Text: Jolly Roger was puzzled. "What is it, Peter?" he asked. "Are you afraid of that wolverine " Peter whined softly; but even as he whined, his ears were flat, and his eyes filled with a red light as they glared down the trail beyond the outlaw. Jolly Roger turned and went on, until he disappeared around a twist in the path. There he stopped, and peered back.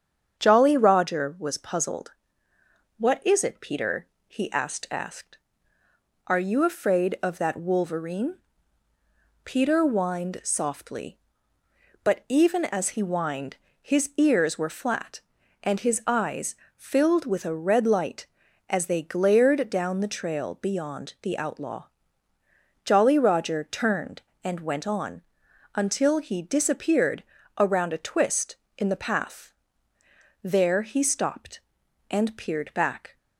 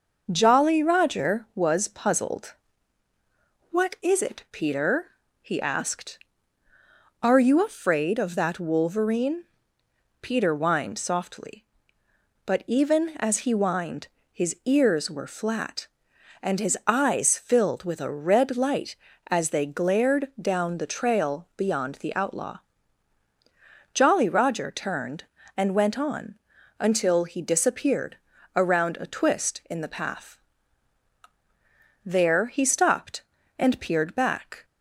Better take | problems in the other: second | starts louder than the rest; strong; until 1.4 s; 8.5 dB // says "asked" twice; at 4.9 s // pauses between "eyes" and "filled"; slight; at 16.5 s; 0.22 s long // pauses between "disappeared" and "around"; slight; at 27.2 s; 0.36 s long; also in the second

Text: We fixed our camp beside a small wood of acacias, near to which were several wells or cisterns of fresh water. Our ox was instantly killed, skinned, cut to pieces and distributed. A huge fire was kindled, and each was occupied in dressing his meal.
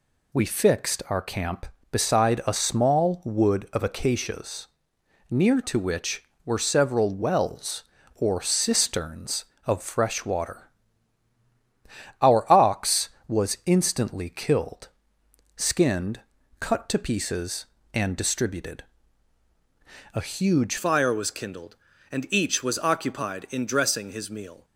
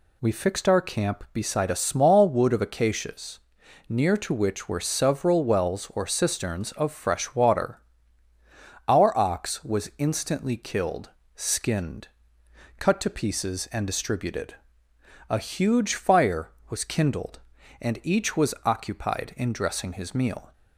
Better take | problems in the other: second | changes voice at "fire"; from 20.7 s on; 3.9 s long

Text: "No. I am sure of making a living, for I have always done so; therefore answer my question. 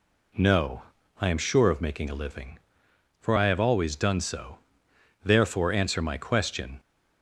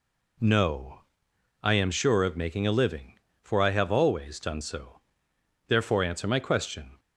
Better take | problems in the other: neither | none

